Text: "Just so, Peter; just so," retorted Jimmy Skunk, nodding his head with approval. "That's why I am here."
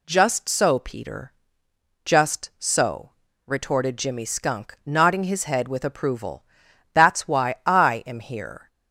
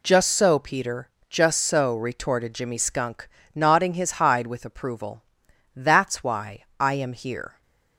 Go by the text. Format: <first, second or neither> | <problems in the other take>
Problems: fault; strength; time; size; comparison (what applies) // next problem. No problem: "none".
first | says "hide" for "head"; at 4.1 s // pauses between "why" and "I"; slight; at 6.6 s; 0.16 s long